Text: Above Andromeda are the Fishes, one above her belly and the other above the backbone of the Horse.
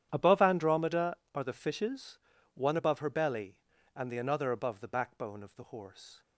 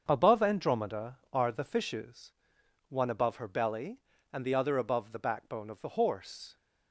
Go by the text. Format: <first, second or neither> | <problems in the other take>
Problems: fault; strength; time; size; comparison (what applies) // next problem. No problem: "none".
second | starts louder than the rest; strong; until 1.1 s; 10 dB; also in the second // says "another" for "other"; at 4.1 s